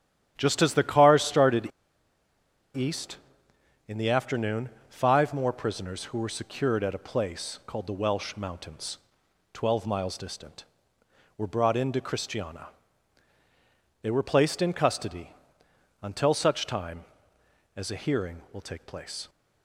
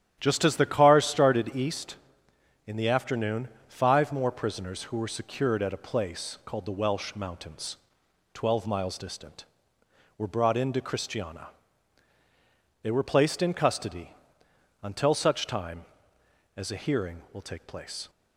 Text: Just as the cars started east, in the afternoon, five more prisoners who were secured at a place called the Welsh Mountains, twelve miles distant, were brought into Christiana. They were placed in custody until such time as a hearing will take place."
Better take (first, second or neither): second